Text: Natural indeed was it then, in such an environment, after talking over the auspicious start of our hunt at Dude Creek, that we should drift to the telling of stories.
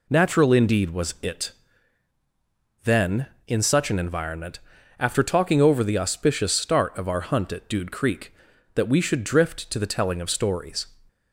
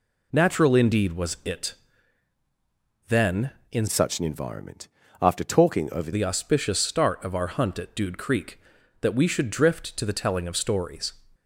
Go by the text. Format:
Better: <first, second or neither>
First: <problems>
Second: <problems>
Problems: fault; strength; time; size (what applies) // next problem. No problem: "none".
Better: first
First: pauses between "it" and "then"; strong; at 1.5 s; 1.3 s long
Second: pauses between "it" and "then"; strong; at 1.7 s; 1.3 s long // changes voice from "such" to "over"; from 3.8 to 6.1 s; 2.3 s long